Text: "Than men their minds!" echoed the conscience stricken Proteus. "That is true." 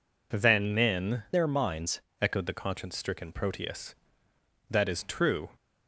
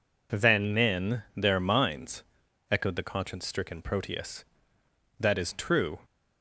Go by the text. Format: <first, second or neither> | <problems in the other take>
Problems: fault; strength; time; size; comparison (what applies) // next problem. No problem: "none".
second | changes voice from "their" to "minds"; from 1.3 to 1.9 s; 0.6 s long